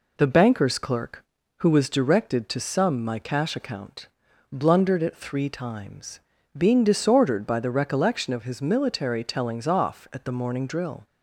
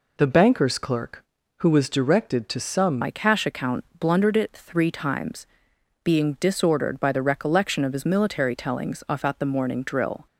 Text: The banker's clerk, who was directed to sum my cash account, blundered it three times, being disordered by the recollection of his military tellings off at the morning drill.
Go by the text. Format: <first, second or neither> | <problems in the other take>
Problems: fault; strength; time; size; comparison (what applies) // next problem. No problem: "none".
first | changes voice at "my"; from 3.0 s on; 7.2 s long